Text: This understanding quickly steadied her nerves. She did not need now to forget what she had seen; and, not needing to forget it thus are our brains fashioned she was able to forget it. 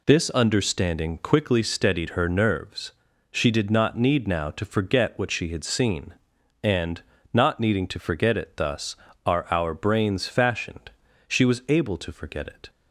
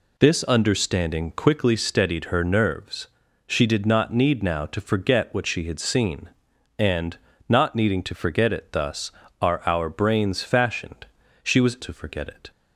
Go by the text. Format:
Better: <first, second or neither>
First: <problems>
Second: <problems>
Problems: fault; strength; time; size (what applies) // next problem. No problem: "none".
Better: first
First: pauses between "fashioned" and "she"; at 10.8 s; 0.38 s long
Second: pauses between "fashioned" and "she"; at 11.0 s; 0.38 s long // skips "able"; at 11.7 s